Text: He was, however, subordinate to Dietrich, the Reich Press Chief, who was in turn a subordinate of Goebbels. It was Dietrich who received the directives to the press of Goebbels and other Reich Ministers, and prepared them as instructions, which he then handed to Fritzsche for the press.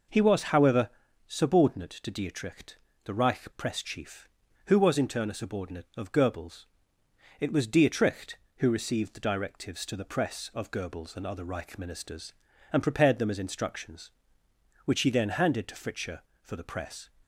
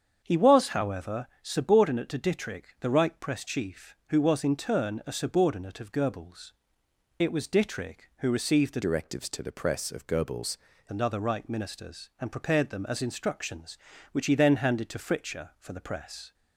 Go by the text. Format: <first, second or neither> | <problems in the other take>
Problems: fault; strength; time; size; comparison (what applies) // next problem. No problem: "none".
first | starts louder than the rest; strong; until 1.2 s; 7.5 dB // changes voice from "directives" to "Goebbels"; from 8.8 to 10.5 s; 1.7 s long